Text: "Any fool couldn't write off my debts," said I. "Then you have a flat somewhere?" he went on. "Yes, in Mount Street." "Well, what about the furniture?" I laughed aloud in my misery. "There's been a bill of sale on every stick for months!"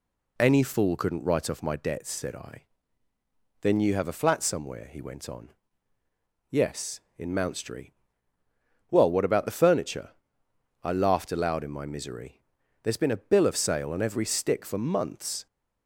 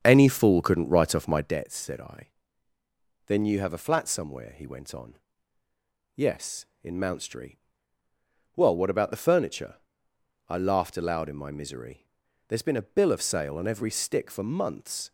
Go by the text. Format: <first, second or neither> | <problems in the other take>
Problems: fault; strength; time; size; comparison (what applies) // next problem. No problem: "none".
first | starts louder than the rest; strong; until 1.7 s; 7.5 dB